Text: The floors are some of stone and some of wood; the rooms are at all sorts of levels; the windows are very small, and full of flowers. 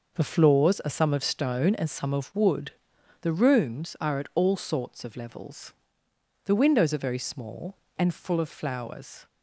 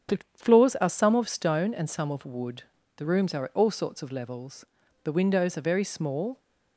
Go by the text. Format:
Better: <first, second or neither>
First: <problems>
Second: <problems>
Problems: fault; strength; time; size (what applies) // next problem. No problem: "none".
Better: first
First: none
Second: starts louder than the rest; strong; until 1.2 s; 8 dB // pauses between "The" and "floors"; slight; at 0.1 s; 0.18 s long // stops before "and full of flowers"; at 6.3 s